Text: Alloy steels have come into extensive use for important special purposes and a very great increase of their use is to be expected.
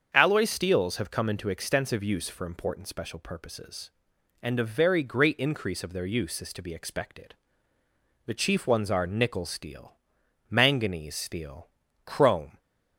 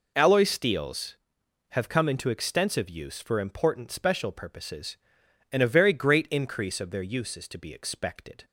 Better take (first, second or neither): second